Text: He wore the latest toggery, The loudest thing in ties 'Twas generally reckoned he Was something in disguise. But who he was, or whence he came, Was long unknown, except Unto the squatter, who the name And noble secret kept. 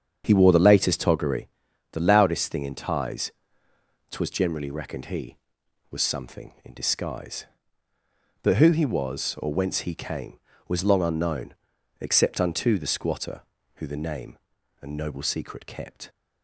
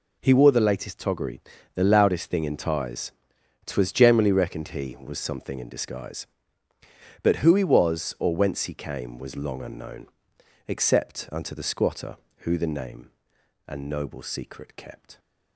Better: second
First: starts louder than the rest; strong; until 1.2 s; 7.5 dB // pauses between "ties" and "Twas"; noticeable; at 3.2 s; 0.80 s long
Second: pauses between "ties" and "Twas"; noticeable; at 3.1 s; 0.54 s long

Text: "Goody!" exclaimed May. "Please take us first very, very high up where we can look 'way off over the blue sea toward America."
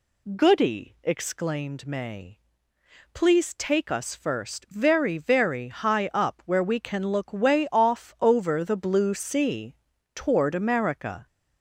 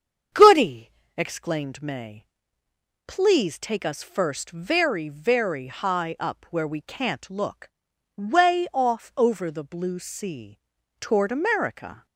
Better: first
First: pauses between "sea" and "toward"; at 9.7 s; 0.40 s long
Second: starts louder than the rest; strong; until 1.6 s; 7.5 dB // says "can't" for "can"; at 6.8 s // pauses between "look" and "way"; noticeable; at 7.6 s; 0.48 s long // pauses between "sea" and "toward"; at 10.5 s; 0.42 s long

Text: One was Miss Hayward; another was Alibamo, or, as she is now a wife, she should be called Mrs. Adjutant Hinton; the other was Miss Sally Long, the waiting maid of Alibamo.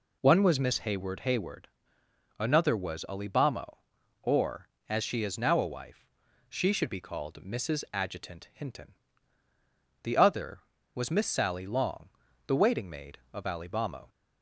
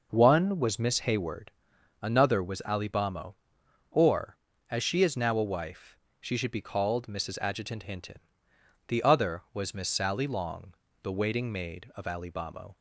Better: second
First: says "Hayward" twice; at 1.2 s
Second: none

